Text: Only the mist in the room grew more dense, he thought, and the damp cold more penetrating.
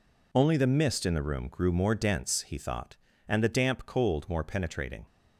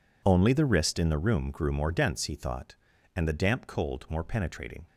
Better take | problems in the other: first | says "wrist" for "mist"; at 0.6 s

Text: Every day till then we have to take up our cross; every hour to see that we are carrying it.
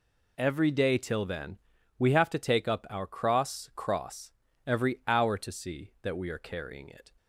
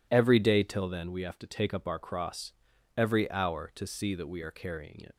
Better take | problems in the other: second | pauses between "then" and "we"; at 1.5 s; 0.42 s long // says "cross" twice; at 3.7 s

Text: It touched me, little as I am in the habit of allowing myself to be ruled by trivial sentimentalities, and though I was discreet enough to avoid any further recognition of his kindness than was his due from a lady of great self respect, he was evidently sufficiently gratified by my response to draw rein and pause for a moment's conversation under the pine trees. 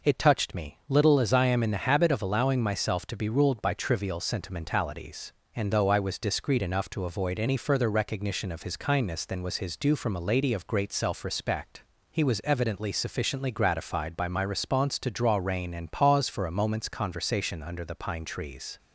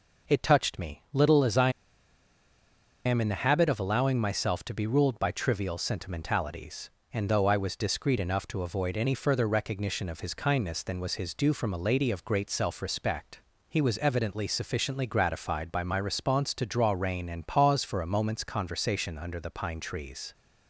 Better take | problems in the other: first | pauses between "I" and "am"; strong; at 1.6 s; 1.3 s long

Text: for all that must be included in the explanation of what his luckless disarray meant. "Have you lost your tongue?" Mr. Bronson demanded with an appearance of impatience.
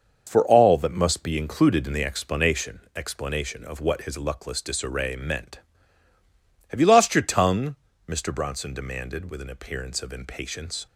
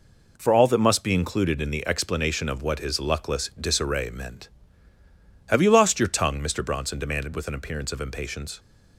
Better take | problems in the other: second | starts louder than the rest; noticeable; until 1.2 s; 6 dB // says "explanation" twice; at 2.9 s

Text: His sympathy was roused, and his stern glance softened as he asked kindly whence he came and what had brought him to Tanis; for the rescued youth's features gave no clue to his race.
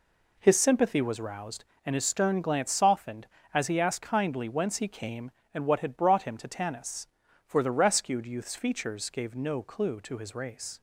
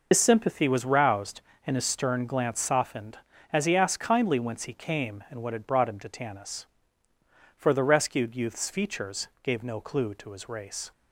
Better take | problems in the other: first | loses the start of "His"; at 0.1 s; 80 ms

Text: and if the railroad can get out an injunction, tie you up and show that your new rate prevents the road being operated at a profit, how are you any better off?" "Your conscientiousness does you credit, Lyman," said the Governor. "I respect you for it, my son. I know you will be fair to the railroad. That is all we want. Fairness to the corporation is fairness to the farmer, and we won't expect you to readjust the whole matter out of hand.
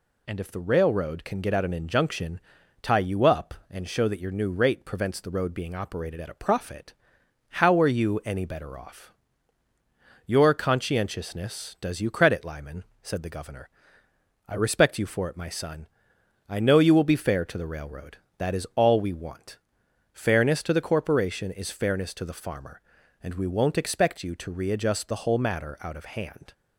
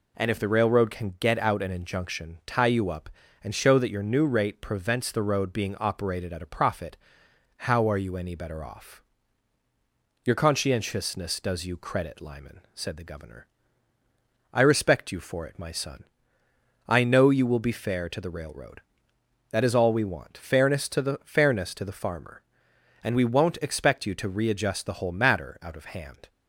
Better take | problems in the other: first | skips "corporation is"; at 21.2 s

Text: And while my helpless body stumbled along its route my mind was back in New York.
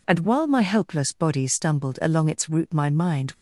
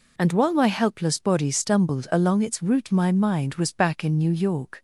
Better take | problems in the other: second | stops before "was back in New York"; at 3.3 s

